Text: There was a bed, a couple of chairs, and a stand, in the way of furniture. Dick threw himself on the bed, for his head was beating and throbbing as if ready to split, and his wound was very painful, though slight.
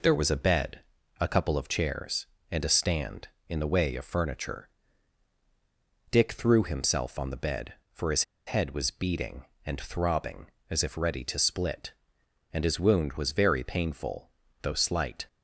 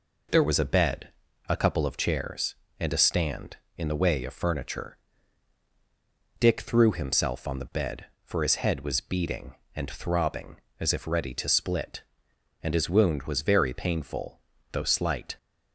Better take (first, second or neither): second